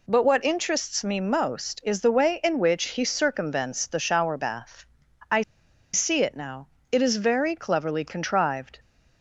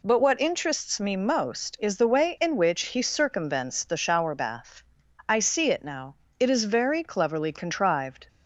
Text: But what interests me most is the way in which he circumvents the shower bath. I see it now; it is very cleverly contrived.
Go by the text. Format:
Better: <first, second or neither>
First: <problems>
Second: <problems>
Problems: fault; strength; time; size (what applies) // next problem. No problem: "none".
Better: second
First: pauses between "I" and "see"; noticeable; at 5.4 s; 0.51 s long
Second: none